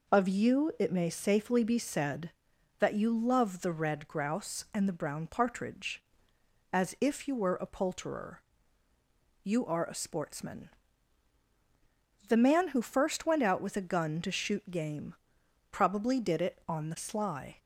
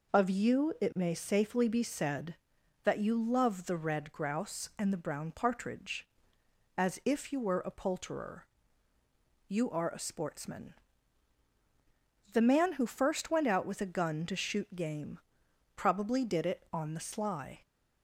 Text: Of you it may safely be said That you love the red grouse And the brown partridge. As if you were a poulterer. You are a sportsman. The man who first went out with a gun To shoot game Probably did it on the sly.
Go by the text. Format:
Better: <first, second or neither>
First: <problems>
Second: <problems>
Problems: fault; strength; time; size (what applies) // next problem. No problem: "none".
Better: neither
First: pauses between "game" and "Probably"; noticeable; at 15.1 s; 0.58 s long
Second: pauses between "game" and "Probably"; noticeable; at 15.1 s; 0.58 s long